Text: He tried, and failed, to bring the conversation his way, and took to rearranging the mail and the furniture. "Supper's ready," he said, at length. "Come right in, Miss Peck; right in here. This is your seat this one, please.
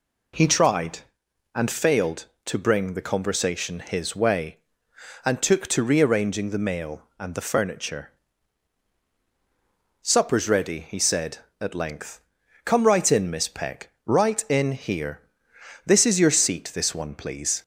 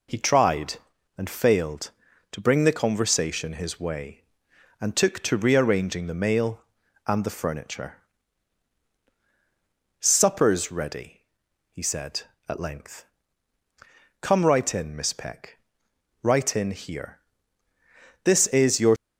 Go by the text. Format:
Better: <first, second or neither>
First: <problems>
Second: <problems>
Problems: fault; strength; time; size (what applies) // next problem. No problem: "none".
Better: first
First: none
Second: stops before "seat this one please"; at 18.9 s